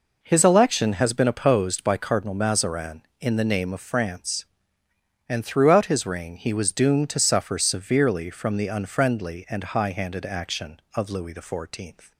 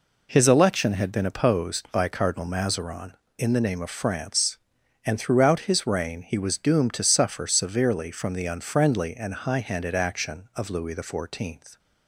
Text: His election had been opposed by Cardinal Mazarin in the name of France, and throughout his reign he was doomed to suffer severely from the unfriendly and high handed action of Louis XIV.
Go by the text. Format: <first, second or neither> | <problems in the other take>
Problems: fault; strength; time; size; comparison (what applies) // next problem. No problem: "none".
second | says "has" for "had"; at 0.9 s